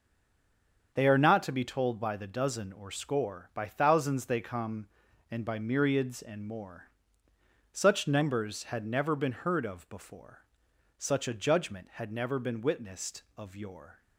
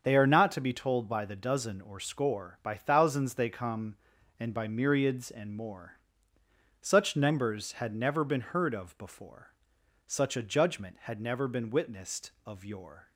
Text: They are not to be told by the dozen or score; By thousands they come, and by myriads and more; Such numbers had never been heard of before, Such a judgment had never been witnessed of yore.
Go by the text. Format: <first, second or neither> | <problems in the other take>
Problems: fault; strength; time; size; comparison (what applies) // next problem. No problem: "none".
second | stays silent before the first word; slight; until 0.9 s; 0.9 s long // starts louder than the rest; until 1.9 s; 7 dB; also in the second